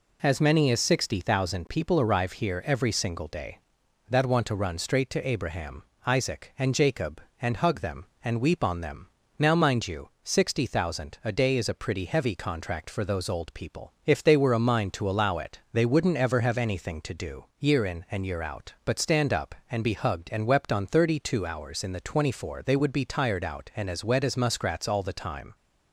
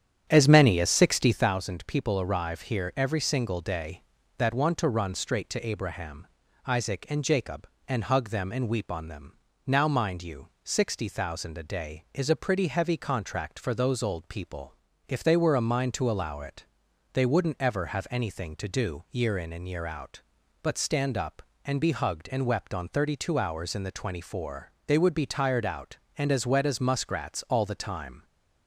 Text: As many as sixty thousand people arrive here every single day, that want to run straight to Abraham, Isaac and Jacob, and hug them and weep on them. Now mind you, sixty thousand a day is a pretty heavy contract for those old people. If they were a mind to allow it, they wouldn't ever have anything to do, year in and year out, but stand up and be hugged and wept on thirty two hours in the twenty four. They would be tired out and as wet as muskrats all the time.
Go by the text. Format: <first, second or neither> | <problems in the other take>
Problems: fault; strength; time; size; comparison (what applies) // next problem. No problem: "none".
first | starts louder than the rest; strong; until 1.5 s; 9.5 dB